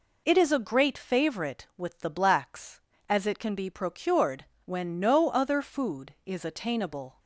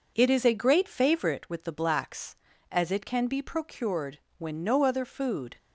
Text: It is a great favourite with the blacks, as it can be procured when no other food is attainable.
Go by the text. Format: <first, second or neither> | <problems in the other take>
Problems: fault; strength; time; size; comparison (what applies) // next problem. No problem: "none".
first | pauses between "procured" and "when"; slight; at 4.1 s; 0.20 s long; slight in the first // stops before "is attainable"; at 5.5 s